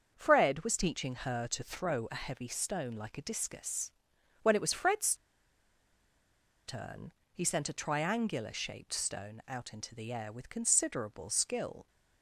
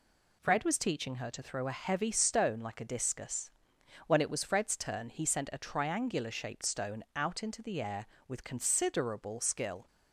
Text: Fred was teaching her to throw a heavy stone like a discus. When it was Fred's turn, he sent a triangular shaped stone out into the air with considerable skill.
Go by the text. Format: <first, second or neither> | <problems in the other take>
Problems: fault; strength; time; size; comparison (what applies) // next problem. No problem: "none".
second | starts louder than the rest; until 1.1 s; 6.5 dB // pauses between "Fred's" and "turn"; strong; at 5.1 s; 1.5 s long